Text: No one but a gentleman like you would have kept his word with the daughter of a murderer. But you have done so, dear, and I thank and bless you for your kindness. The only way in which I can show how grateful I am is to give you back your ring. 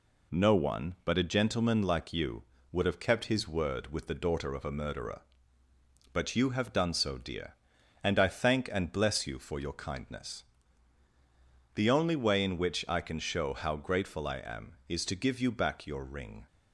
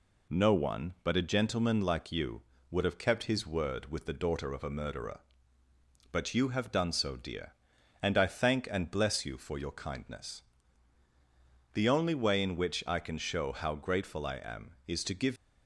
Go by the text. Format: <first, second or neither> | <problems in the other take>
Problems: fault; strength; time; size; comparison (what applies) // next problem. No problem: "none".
first | stops before "you back your ring"; at 15.3 s